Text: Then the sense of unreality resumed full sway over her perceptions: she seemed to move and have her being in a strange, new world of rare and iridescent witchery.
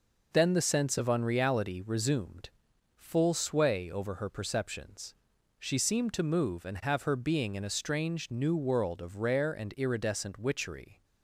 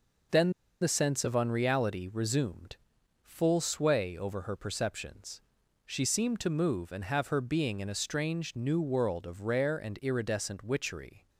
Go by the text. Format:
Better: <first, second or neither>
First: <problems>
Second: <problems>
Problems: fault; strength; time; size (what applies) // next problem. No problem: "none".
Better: first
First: pauses between "resumed" and "full"; noticeable; at 2.4 s; 0.48 s long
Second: pauses between "Then" and "the"; slight; at 0.5 s; 0.28 s long // pauses between "resumed" and "full"; noticeable; at 2.7 s; 0.48 s long